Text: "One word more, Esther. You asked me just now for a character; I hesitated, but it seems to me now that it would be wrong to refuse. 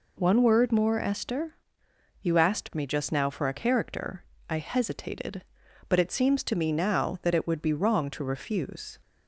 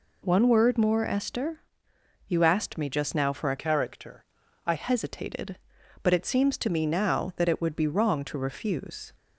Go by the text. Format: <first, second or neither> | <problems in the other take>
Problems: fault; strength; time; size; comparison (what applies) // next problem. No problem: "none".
first | changes voice from "character" to "I"; from 3.5 to 4.7 s; 1.2 s long